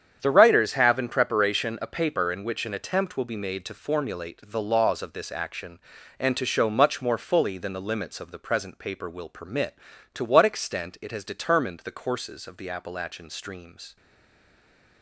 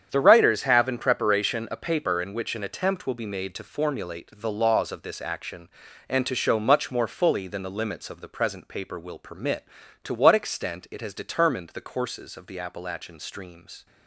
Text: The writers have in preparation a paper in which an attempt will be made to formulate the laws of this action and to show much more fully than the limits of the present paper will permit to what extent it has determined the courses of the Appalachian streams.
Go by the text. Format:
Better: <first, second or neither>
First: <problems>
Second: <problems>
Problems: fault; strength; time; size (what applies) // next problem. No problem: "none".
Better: second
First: starts louder than the rest; strong; until 1.2 s; 8.5 dB // stays silent after the last word; from 13.9 s on; 1.1 s long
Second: starts louder than the rest; strong; until 1.1 s; 8.5 dB